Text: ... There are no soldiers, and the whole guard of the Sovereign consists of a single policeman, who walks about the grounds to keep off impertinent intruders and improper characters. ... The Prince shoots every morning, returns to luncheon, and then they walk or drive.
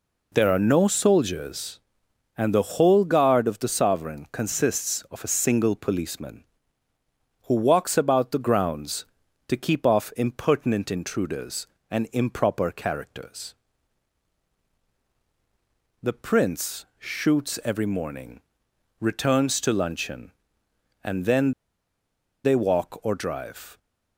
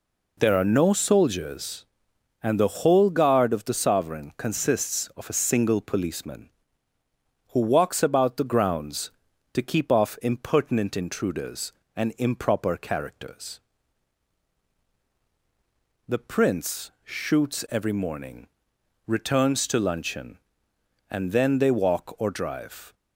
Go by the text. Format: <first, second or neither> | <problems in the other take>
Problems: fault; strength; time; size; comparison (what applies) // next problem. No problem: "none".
second | pauses between "then" and "they"; noticeable; at 21.5 s; 0.93 s long